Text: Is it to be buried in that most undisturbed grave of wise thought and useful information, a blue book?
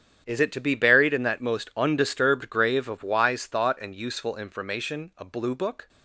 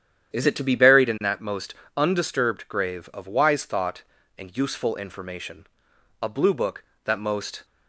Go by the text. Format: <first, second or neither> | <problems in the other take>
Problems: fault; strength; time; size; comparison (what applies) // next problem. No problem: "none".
first | starts louder than the rest; strong; until 1.3 s; 9.5 dB; strong in the first // pauses between "most" and "undisturbed"; slight; at 1.7 s; 0.20 s long // goes on to say "that most"; from 7.0 s on; 0.60 s long